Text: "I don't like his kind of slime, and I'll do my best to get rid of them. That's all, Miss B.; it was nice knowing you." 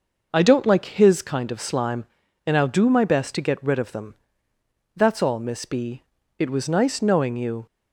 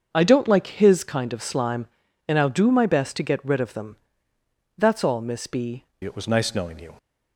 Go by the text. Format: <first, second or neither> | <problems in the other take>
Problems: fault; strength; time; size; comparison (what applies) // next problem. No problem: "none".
first | starts louder than the rest; until 1.1 s; 6.5 dB // changes voice at "it"; from 6.0 s on; 0.9 s long